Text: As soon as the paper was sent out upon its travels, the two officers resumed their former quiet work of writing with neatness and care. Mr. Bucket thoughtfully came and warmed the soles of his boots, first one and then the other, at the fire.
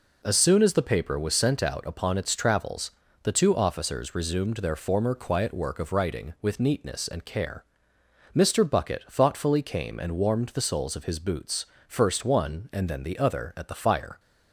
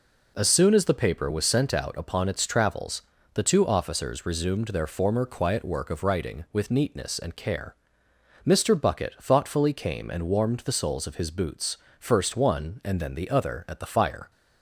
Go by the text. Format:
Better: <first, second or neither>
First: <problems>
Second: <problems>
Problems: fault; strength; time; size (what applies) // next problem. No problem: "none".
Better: neither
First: none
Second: none